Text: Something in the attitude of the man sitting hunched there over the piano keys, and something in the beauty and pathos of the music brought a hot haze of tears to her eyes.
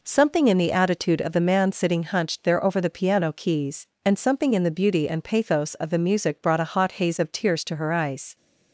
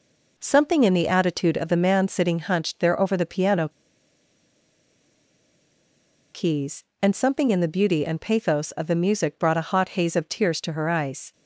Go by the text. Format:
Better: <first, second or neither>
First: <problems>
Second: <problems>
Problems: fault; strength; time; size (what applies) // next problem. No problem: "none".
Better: first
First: none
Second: pauses between "piano" and "keys"; strong; at 3.6 s; 2.6 s long